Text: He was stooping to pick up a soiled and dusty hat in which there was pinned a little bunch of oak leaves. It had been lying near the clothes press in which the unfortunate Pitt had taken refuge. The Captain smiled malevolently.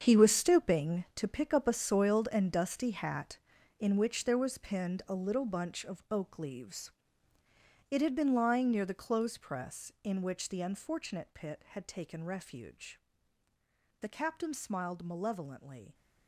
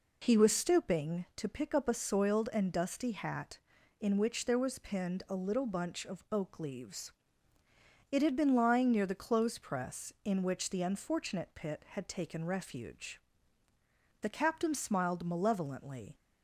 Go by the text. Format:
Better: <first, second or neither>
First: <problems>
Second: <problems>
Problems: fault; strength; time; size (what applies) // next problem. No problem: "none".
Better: second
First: gets quieter; strong; throughout; 13 dB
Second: none